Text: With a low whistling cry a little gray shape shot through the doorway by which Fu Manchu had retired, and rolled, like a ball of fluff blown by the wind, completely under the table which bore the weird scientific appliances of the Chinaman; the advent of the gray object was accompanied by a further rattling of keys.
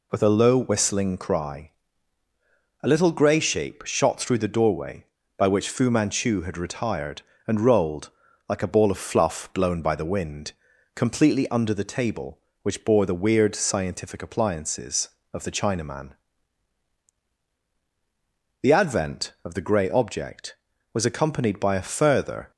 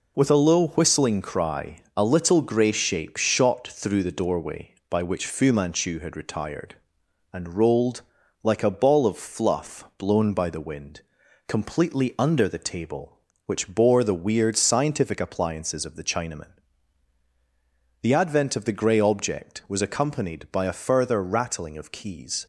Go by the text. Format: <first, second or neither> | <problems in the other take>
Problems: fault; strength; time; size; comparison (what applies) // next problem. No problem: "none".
second | pauses between "cry" and "a"; at 1.7 s; 1.1 s long // stops before "rattling of keys"; at 22.5 s